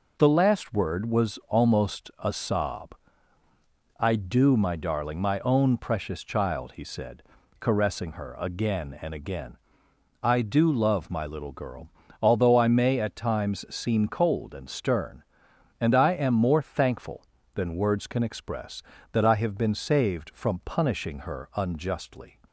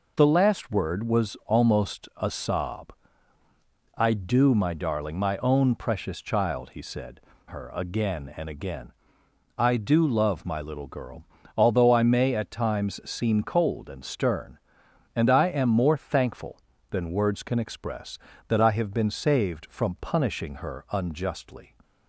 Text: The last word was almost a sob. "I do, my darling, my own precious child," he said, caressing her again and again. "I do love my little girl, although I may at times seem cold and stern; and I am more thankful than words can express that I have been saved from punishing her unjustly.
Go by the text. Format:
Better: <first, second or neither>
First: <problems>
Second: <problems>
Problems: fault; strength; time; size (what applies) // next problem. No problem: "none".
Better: first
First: none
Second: skips "caressing"; at 7.3 s